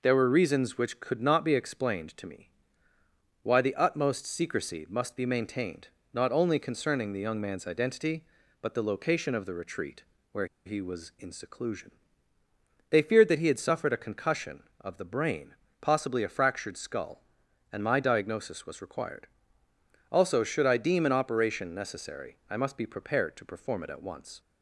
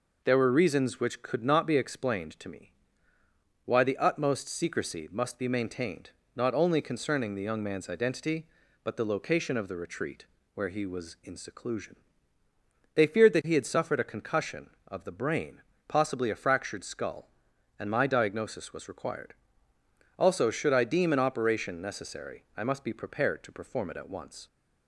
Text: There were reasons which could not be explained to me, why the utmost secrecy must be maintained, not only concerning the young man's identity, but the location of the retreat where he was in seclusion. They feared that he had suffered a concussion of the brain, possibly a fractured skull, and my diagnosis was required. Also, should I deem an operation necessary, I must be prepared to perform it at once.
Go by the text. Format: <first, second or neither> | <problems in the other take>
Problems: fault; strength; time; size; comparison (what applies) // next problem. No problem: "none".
second | pauses between "retreat" and "where"; slight; at 10.0 s; 0.26 s long; slight in the second // pauses between "where" and "he"; slight; at 10.4 s; 0.19 s long